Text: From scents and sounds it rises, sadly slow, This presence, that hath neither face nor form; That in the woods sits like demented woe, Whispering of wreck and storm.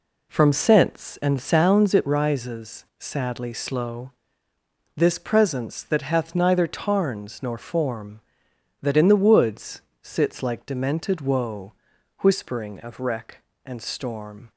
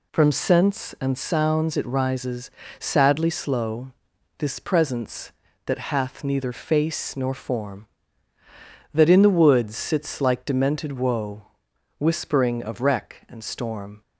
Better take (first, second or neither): second